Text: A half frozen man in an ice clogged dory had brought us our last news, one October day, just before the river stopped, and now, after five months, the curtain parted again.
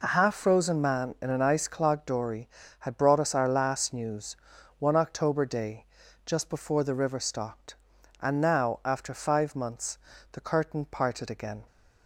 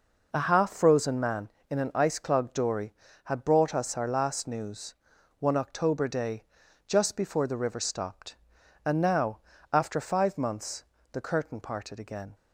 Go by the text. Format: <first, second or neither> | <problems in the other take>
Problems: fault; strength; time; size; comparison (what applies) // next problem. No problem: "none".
neither | none